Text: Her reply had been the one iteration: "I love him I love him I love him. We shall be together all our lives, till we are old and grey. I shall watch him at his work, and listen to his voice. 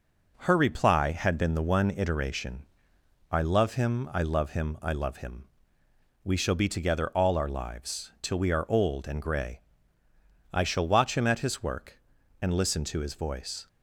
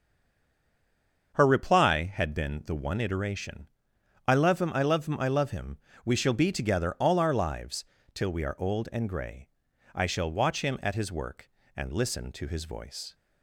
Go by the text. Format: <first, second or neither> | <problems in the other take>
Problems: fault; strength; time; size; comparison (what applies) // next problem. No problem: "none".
first | stays silent before the first word; noticeable; until 1.3 s; 1.3 s long // starts louder than the rest; until 2.3 s; 6.5 dB